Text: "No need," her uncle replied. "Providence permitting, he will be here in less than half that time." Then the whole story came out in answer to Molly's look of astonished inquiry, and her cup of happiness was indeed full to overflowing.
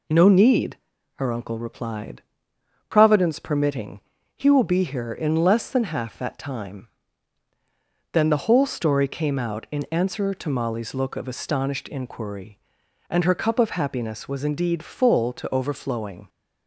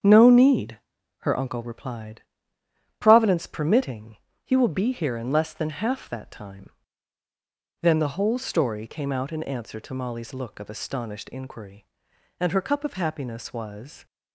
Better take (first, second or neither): first